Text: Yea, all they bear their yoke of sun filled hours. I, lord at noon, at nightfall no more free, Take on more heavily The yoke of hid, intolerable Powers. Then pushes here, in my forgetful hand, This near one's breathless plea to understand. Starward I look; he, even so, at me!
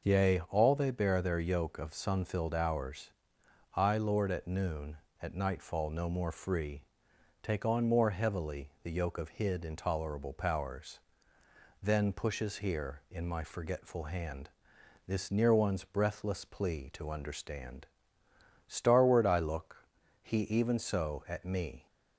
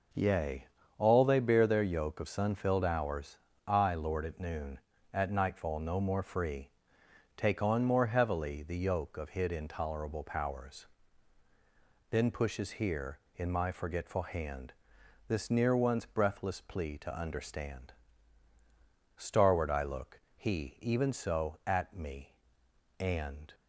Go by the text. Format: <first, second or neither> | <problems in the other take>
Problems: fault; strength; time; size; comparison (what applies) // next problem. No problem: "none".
first | goes on to say "And"; from 23.0 s on; 0.54 s long